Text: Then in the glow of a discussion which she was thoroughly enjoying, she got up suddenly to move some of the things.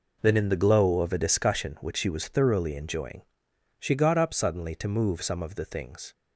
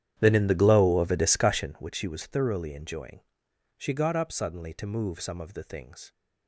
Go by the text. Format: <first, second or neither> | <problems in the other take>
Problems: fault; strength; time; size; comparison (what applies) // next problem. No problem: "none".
first | starts louder than the rest; strong; until 1.9 s; 10 dB